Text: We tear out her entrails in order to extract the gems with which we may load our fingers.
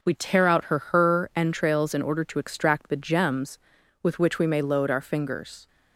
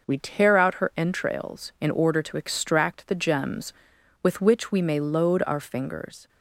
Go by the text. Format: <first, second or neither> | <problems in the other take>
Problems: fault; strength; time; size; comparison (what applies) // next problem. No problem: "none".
second | says "her" twice; at 0.7 s